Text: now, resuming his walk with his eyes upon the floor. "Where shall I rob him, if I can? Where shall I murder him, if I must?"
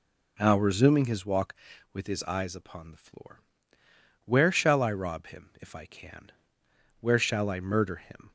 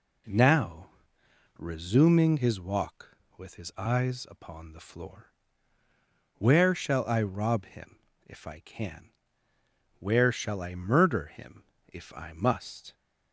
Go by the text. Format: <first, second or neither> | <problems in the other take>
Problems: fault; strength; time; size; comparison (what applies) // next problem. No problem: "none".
second | stops before "if I must"; at 8.2 s